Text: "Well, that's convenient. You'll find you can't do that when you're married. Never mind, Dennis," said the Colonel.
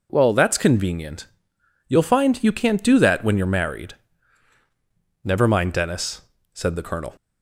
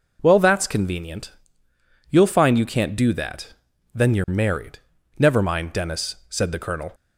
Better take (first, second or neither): first